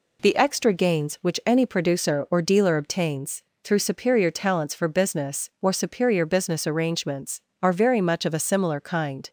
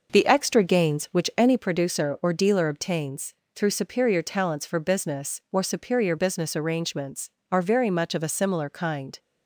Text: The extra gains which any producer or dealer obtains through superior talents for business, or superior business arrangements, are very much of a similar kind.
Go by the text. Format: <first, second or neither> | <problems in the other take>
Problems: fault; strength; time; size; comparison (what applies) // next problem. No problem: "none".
first | starts louder than the rest; noticeable; until 1.7 s; 5.5 dB // pauses between "obtains" and "through"; slight; at 3.3 s; 0.22 s long; slight in the first